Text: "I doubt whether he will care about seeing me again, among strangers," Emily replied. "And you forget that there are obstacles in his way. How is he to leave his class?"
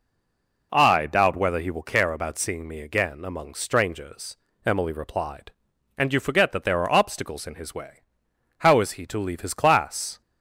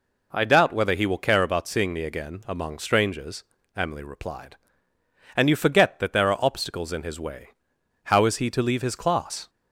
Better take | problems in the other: second | stays silent before the first word; slight; until 0.7 s; 0.7 s long

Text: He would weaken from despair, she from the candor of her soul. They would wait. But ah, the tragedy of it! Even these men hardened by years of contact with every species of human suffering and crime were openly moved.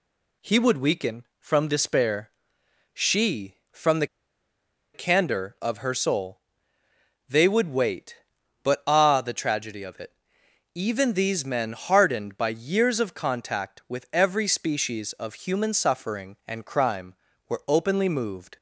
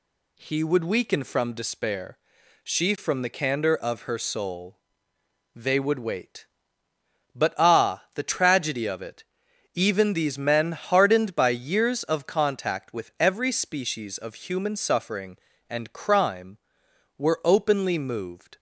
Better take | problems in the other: second | pauses between "the" and "candor"; noticeable; at 4.0 s; 0.87 s long

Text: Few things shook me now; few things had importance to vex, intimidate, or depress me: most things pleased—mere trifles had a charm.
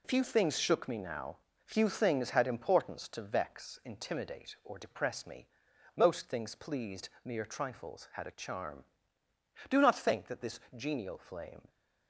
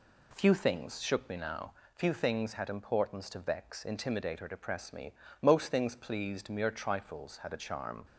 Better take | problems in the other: second | goes on to say "Do not think that this genial flame"; strong; from 9.6 s on; 2.0 s long

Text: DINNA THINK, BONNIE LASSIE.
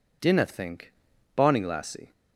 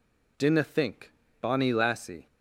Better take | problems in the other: neither | none

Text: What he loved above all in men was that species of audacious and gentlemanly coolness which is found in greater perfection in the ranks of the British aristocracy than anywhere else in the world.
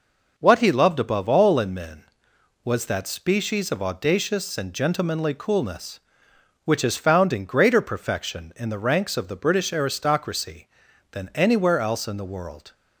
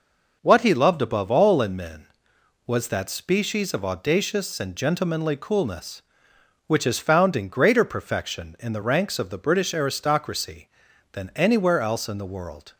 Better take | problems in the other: neither | none

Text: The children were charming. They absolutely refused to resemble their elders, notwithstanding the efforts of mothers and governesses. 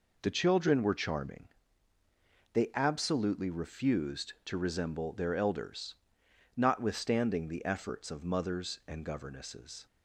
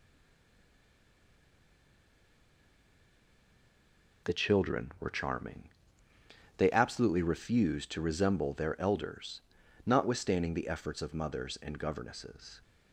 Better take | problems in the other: first | stays silent before the first word; strong; until 4.2 s; 4.2 s long

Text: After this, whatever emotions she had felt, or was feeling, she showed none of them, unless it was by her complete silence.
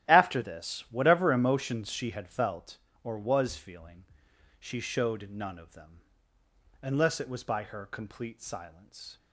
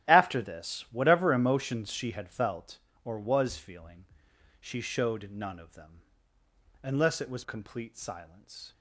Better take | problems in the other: first | starts louder than the rest; strong; until 1.1 s; 13 dB; strong in the first // skips "by her"; at 7.4 s

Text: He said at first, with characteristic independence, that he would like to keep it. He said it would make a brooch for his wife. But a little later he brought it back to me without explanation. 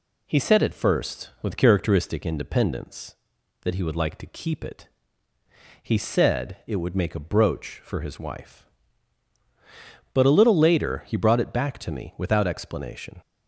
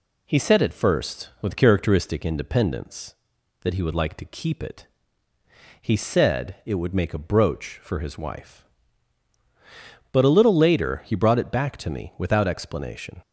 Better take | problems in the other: neither | none

